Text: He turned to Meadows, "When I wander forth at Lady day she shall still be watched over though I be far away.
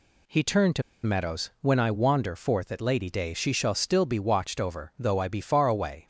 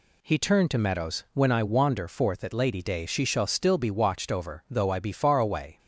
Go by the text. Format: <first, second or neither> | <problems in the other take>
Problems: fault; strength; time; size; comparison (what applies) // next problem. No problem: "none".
second | pauses between "to" and "Meadows"; slight; at 0.8 s; 0.22 s long